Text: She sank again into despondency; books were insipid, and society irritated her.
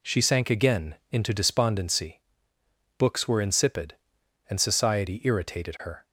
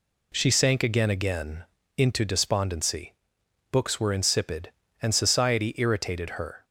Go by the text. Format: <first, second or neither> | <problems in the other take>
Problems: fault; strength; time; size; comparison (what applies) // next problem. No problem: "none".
first | says "again" twice; at 1.1 s